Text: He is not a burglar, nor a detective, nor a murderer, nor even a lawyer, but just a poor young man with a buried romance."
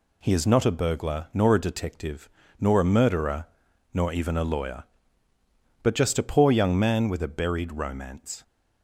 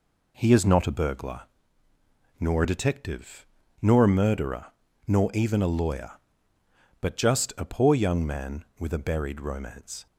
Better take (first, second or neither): neither